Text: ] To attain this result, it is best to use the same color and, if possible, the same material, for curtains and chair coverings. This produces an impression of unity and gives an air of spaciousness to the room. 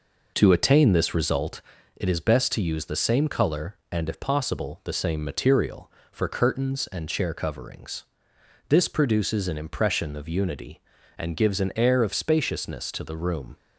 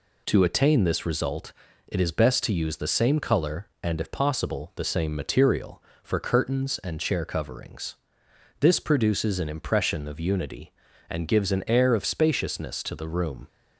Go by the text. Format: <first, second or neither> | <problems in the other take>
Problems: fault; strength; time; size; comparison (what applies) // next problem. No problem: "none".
second | starts louder than the rest; noticeable; until 1.9 s; 5 dB